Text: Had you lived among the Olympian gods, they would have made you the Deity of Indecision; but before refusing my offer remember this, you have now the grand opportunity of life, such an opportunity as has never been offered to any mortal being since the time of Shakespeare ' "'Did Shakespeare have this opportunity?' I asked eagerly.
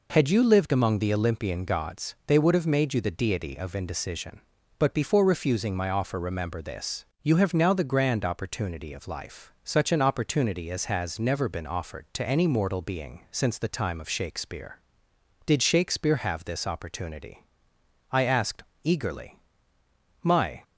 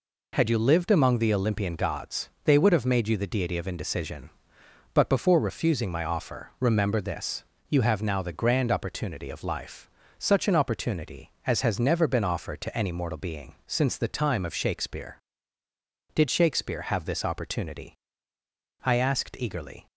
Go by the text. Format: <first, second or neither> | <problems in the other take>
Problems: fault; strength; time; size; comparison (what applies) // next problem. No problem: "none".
second | pauses between "asked" and "eagerly"; slight; at 18.6 s; 0.20 s long // goes on to say "My"; slight; from 20.2 s on; 0.40 s long